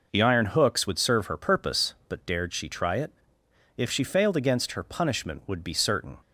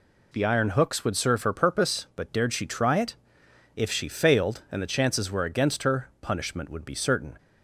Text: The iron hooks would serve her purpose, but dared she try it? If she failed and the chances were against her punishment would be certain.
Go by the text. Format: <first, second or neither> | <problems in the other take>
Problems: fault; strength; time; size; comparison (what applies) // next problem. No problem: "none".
second | skips "and the chances were"; at 4.3 s